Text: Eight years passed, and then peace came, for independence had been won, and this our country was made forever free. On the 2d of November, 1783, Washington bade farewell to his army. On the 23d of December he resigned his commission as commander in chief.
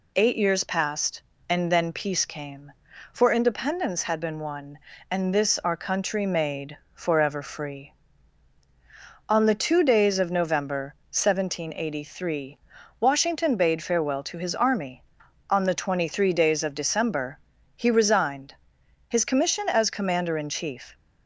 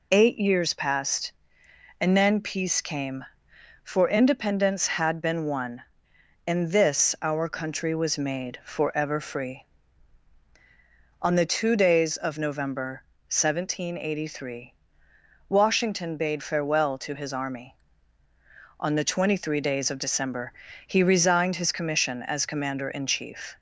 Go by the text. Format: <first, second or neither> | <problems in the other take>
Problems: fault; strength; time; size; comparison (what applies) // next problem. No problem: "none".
second | skips "was"; at 6.2 s // pauses between "made" and "forever"; slight; at 6.7 s; 0.20 s long // pauses between "December" and "he"; at 17.3 s; 0.38 s long; slight in the second // pauses between "resigned" and "his"; noticeable; at 18.5 s; 0.54 s long